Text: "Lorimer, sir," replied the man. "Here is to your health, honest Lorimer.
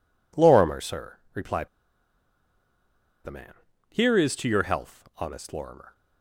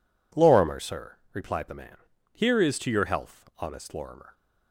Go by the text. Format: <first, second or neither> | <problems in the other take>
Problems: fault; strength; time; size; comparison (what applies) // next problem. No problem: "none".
second | pauses between "replied" and "the"; strong; at 1.6 s; 1.5 s long